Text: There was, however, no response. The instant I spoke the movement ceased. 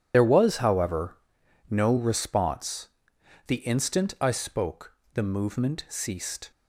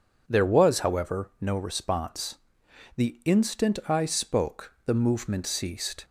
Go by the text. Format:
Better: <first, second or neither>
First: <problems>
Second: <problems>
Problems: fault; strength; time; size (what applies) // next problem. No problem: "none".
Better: second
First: loses the start of "There"; at 0.1 s; 60 ms // pauses between "spoke" and "the"; slight; at 4.9 s; 0.22 s long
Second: none